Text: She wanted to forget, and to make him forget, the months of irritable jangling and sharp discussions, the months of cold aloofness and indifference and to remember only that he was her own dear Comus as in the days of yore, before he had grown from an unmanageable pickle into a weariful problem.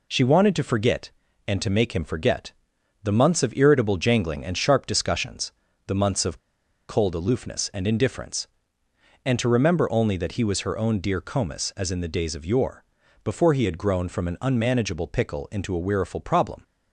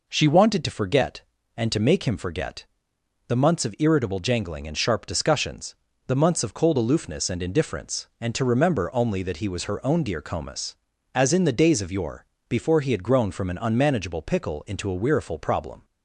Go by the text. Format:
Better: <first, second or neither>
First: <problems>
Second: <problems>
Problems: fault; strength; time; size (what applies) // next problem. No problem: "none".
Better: second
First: pauses between "of" and "cold"; noticeable; at 6.3 s; 0.50 s long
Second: none